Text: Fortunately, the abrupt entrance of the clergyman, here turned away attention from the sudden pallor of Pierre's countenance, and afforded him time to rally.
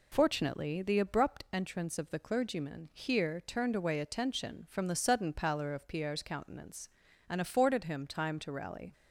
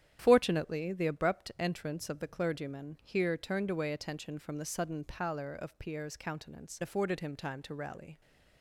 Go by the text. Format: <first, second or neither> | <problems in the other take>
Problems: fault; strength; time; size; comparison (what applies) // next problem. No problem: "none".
first | starts louder than the rest; strong; until 1.2 s; 10 dB // skips "and"; at 6.8 s